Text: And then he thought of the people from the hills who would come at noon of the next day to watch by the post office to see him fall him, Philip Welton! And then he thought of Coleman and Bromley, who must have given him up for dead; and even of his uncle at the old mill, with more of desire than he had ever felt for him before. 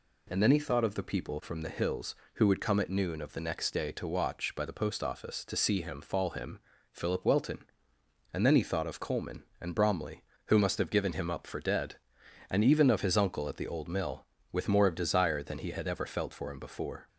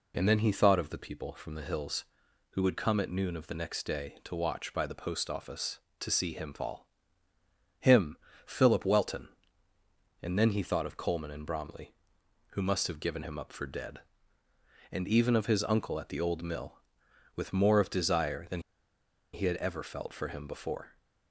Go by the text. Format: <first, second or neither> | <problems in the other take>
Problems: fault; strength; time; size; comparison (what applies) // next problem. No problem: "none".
first | pauses between "fall" and "him"; noticeable; at 6.8 s; 0.92 s long // pauses between "than" and "he"; noticeable; at 18.6 s; 0.71 s long